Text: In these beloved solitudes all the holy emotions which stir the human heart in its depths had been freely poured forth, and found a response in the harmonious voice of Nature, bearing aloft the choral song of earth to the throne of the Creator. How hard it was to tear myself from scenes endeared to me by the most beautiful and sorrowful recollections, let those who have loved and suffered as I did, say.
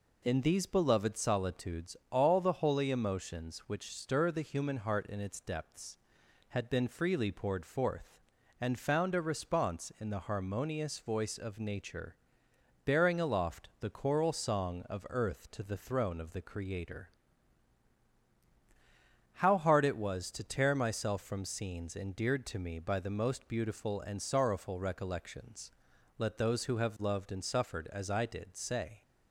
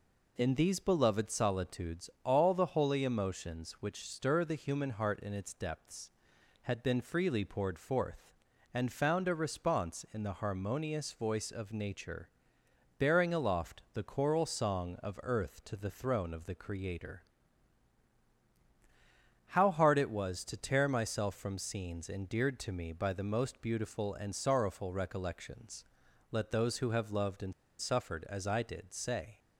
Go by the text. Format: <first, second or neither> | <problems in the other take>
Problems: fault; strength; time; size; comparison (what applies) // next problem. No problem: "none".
first | pauses between "and" and "suffered"; slight; at 27.5 s; 0.27 s long